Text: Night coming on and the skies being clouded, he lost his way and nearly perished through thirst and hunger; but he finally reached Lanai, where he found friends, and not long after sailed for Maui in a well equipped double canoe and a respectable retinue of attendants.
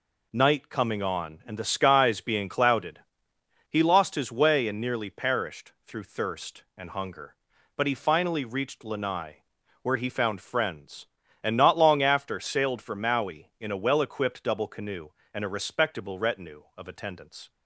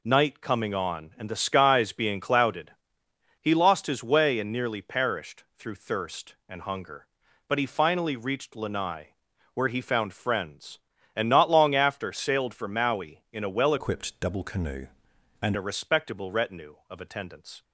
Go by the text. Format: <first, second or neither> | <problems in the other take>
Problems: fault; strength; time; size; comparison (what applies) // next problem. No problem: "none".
first | pauses between "perished" and "through"; slight; at 5.4 s; 0.16 s long; slight in the first // changes voice from "equipped" to "and"; from 13.7 to 15.5 s; 1.8 s long